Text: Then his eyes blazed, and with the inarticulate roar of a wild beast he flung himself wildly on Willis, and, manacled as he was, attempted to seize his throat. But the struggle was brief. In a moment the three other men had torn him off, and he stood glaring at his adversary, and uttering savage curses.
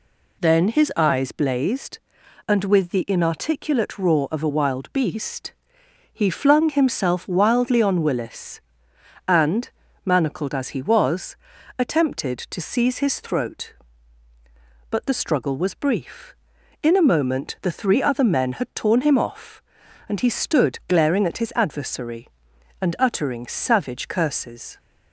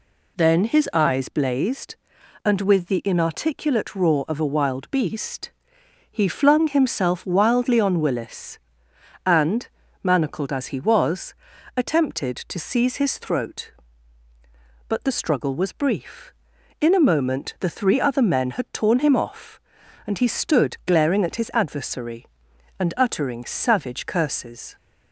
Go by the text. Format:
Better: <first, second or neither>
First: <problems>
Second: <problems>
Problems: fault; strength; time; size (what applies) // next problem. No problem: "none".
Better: neither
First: pauses between "beast" and "he"; noticeable; at 5.5 s; 0.60 s long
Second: pauses between "beast" and "he"; noticeable; at 5.5 s; 0.60 s long